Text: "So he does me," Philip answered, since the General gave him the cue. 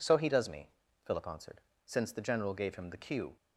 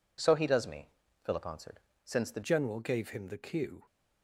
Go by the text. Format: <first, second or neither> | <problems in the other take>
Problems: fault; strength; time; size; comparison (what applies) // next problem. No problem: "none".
first | changes voice at "General"; from 2.4 s on; 1.4 s long